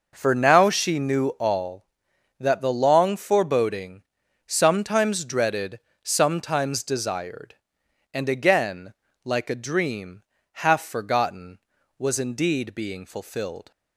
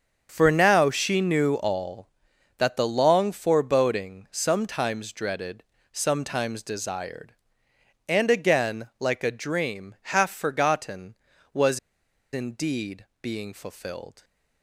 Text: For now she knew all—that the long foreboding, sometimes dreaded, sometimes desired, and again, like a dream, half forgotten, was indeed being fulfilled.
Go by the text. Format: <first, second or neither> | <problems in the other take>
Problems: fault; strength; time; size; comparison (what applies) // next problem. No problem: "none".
first | starts louder than the rest; until 1.3 s; 7 dB // pauses between "was" and "indeed"; noticeable; at 11.7 s; 0.54 s long // pauses between "indeed" and "being"; slight; at 13.0 s; 0.16 s long